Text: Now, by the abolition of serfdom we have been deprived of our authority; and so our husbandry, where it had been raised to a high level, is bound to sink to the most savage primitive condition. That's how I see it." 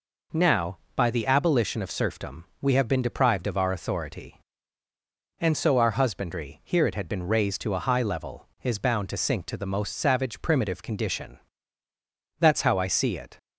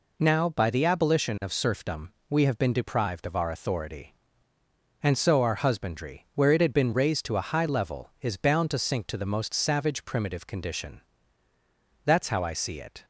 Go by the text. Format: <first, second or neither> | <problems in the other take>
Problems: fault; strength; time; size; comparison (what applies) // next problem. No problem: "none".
second | pauses between "serfdom" and "we"; slight; at 2.4 s; 0.18 s long; slight in the second // says "here" for "where"; at 6.6 s